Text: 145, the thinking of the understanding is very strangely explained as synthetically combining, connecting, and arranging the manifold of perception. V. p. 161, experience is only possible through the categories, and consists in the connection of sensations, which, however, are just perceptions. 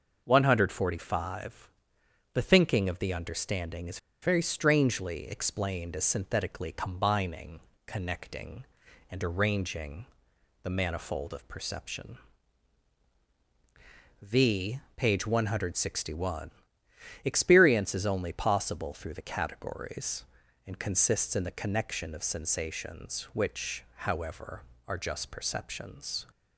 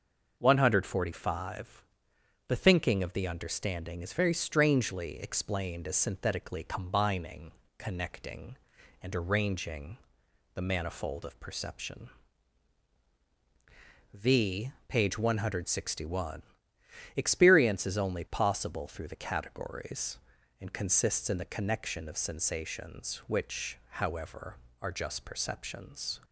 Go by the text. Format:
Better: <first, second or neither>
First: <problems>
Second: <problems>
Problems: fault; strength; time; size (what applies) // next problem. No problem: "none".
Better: second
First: starts louder than the rest; noticeable; until 1.2 s; 6 dB // pauses between "is" and "very"; slight; at 3.9 s; 0.25 s long // pauses between "arranging" and "the"; noticeable; at 10.0 s; 0.58 s long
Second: starts louder than the rest; noticeable; until 1.3 s; 6 dB // pauses between "arranging" and "the"; noticeable; at 9.9 s; 0.58 s long